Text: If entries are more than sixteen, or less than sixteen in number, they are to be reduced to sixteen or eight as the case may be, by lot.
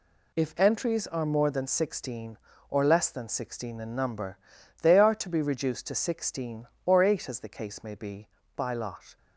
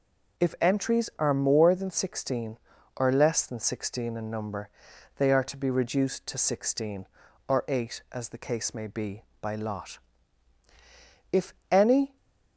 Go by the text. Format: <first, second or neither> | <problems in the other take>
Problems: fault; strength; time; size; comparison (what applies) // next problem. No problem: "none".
first | goes on to say "If any"; noticeable; from 11.3 s on; 0.86 s long